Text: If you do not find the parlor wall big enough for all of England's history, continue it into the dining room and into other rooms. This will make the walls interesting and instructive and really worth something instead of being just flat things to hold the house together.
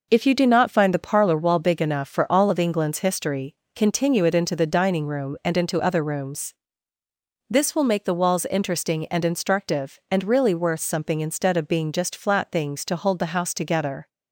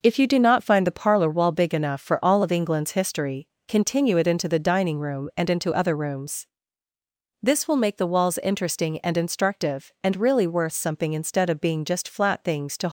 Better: first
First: none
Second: stops before "hold the house together"; at 12.8 s

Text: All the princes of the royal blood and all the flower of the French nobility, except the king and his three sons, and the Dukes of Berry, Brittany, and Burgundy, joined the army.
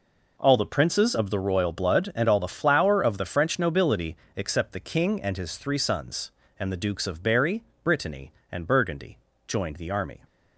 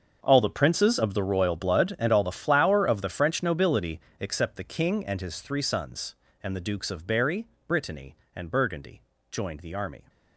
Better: first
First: none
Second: gets quieter; strong; throughout; 16 dB

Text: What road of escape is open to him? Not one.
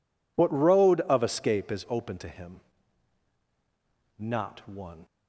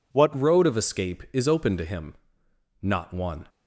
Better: first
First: none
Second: changes voice at "road"; from 0.3 s on; 3.1 s long

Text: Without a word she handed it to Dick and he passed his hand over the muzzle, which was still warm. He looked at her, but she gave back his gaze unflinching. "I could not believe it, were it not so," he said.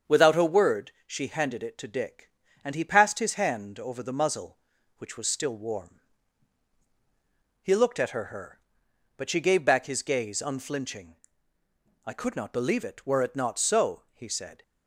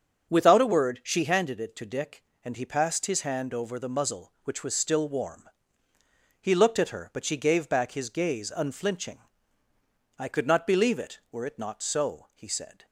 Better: second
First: starts louder than the rest; strong; until 1.2 s; 7 dB // pauses between "word" and "she"; slight; at 0.9 s; 0.15 s long // says "her" twice; at 8.2 s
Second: starts louder than the rest; until 1.3 s; 6.5 dB

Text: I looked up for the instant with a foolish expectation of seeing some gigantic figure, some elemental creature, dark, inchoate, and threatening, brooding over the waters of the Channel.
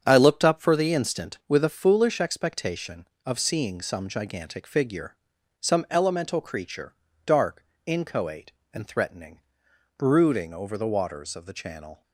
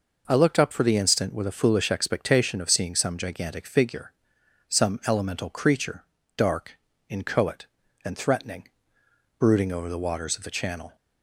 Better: second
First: gets quieter; strong; throughout; 8 dB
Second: none

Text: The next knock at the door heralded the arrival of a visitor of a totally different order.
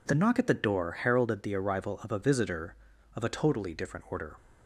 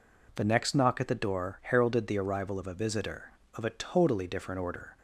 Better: second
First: skips "next"; at 0.1 s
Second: none

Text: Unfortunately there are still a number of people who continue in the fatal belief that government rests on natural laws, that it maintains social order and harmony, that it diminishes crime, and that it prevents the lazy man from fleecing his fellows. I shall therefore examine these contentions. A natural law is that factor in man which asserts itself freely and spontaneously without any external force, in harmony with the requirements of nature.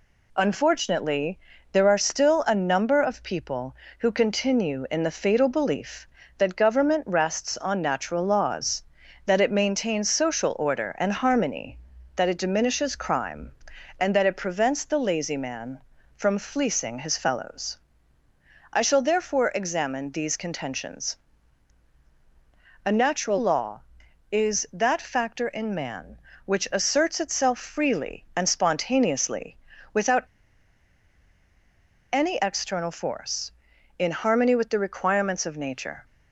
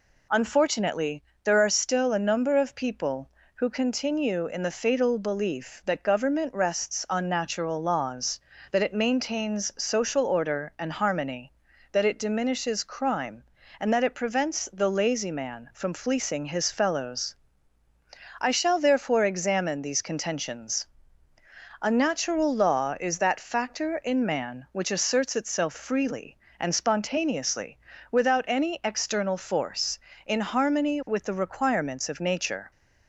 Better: second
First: pauses between "Unfortunately" and "there"; slight; at 1.3 s; 0.34 s long // pauses between "spontaneously" and "without"; slight; at 29.5 s; 0.36 s long // pauses between "without" and "any"; strong; at 30.2 s; 1.9 s long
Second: pauses between "Unfortunately" and "there"; slight; at 1.2 s; 0.22 s long // pauses between "spontaneously" and "without"; slight; at 27.7 s; 0.32 s long

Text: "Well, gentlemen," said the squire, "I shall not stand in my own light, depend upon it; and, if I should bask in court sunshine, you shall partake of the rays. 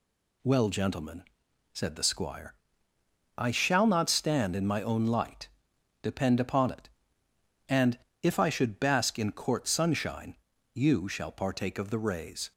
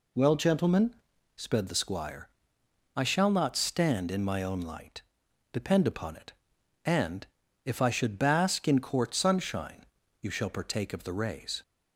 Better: first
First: none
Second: says "sped" for "said"; at 1.3 s

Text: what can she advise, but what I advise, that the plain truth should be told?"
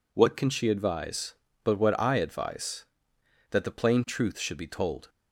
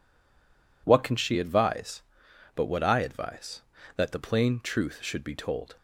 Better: first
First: none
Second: stays silent before the first word; slight; until 0.8 s; 0.8 s long

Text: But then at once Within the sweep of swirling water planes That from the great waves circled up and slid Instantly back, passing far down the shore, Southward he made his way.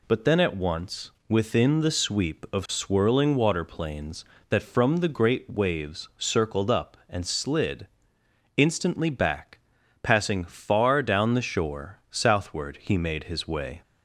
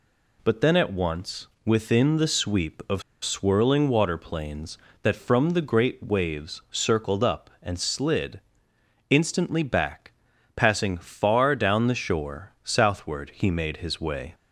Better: first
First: pauses between "slid" and "Instantly"; noticeable; at 7.8 s; 0.68 s long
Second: pauses between "of" and "swirling"; slight; at 3.0 s; 0.21 s long // pauses between "slid" and "Instantly"; noticeable; at 8.4 s; 0.68 s long

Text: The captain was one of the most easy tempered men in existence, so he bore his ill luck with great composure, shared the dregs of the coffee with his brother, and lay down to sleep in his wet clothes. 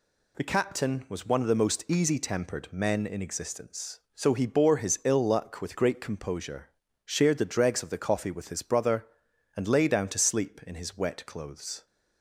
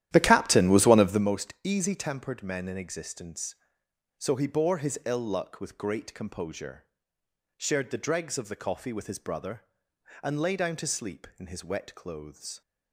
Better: first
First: none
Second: starts louder than the rest; strong; until 1.4 s; 12 dB

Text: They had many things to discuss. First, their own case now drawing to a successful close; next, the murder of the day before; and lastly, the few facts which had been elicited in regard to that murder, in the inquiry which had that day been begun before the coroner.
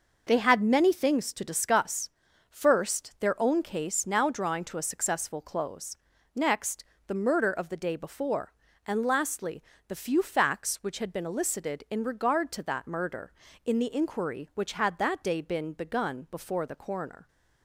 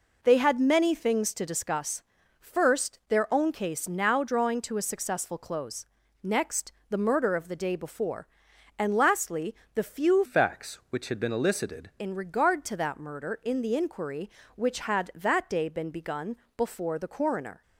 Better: first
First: none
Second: changes voice from "facts" to "elicited"; from 10.2 to 11.8 s; 1.6 s long // pauses between "begun" and "before"; slight; at 16.3 s; 0.20 s long

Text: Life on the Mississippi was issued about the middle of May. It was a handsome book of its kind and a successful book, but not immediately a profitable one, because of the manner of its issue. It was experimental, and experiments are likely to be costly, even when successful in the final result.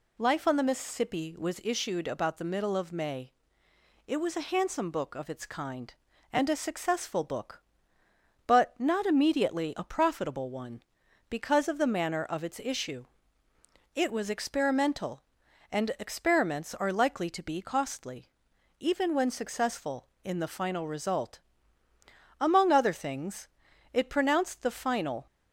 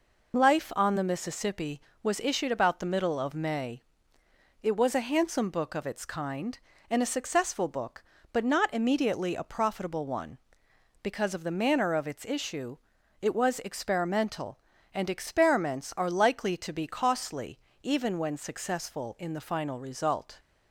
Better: second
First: goes on to say "Among other things it pronounced the final"; strong; from 22.4 s on; 2.8 s long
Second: none

